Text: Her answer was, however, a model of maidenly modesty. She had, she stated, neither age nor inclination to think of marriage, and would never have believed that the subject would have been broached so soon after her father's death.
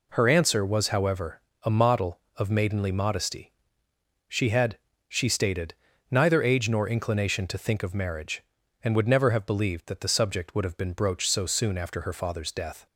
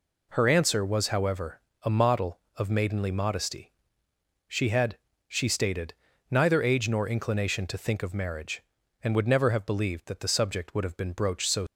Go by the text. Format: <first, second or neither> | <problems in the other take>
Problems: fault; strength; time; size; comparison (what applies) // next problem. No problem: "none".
first | stops before "soon after her father's death"; at 11.6 s